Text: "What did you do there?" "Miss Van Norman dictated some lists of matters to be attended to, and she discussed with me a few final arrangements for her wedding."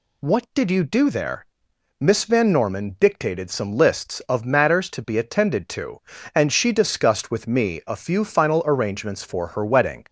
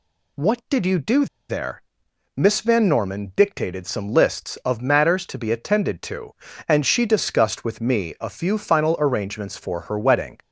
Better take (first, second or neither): first